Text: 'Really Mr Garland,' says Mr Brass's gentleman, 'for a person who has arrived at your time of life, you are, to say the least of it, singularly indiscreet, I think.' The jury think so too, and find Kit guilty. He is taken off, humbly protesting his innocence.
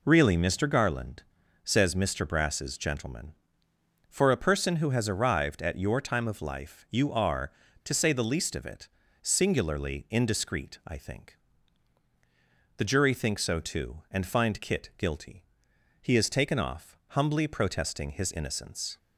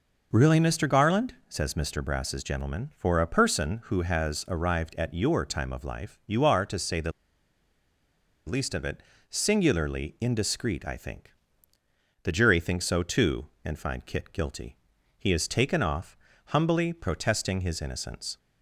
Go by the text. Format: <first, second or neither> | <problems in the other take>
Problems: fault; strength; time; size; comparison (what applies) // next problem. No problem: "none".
first | pauses between "the" and "least"; strong; at 7.1 s; 1.3 s long